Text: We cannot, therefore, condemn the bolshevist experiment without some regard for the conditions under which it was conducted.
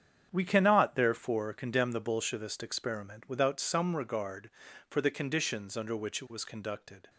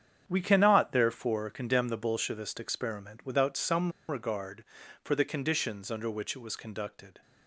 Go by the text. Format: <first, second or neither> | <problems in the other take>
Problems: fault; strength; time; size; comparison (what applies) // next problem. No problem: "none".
first | starts louder than the rest; strong; until 1.2 s; 8 dB; strong in the first // pauses between "some" and "regard"; slight; at 3.9 s; 0.19 s long